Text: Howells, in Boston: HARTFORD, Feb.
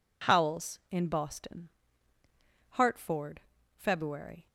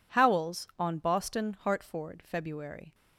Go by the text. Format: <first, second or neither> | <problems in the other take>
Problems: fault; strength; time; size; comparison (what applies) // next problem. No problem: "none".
first | says "on" for "in"; at 0.7 s